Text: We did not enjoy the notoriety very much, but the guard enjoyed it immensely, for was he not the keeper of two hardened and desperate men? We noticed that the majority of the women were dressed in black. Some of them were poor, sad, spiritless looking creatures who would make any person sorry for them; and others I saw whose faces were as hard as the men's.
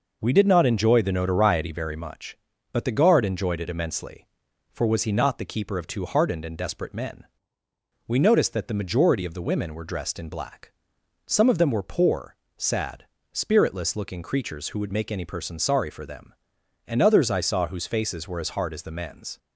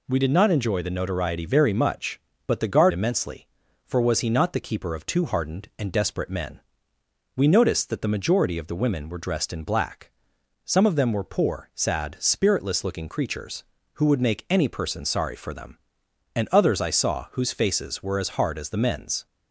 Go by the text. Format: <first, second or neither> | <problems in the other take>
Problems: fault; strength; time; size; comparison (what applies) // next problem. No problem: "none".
first | skips "enjoyed it"; at 2.9 s